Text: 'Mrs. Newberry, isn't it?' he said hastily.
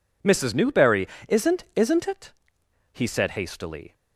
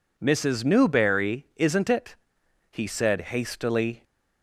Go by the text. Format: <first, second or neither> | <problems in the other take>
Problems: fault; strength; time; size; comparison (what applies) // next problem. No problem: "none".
second | says "isn't" twice; at 1.7 s